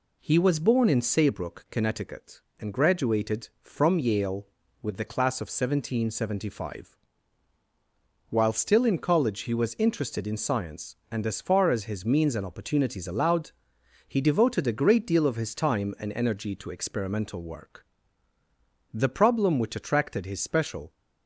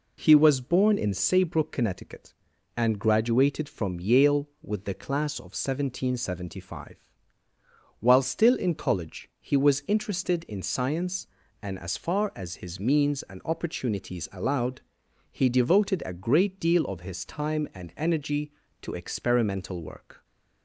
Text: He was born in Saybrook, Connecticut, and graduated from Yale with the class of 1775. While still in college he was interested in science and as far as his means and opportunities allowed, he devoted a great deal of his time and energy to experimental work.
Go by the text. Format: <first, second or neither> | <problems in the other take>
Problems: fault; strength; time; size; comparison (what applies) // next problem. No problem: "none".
second | goes on to say "The problem which attracted his special"; strong; from 18.9 s on; 2.0 s long